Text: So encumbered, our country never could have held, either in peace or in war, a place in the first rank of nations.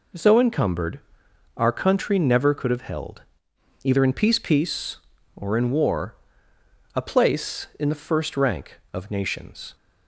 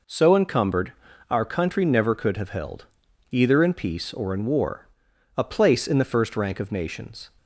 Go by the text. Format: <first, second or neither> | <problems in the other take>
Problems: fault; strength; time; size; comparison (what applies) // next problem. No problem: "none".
second | says "peace" twice; at 4.3 s